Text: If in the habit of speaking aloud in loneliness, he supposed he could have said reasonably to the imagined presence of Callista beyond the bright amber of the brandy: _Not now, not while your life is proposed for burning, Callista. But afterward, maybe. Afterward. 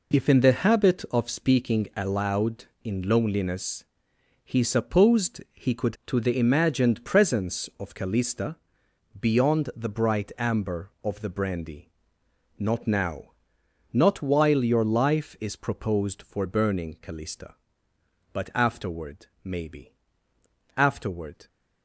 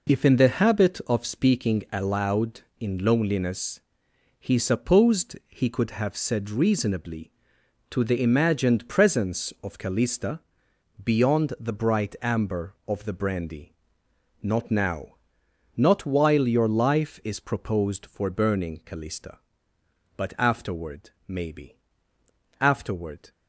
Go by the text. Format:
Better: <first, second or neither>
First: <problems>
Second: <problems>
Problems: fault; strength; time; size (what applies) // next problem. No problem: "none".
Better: second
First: skips "have said reasonably"; at 6.0 s // pauses between "Callista" and "beyond"; noticeable; at 8.5 s; 0.64 s long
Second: pauses between "Callista" and "beyond"; noticeable; at 10.3 s; 0.64 s long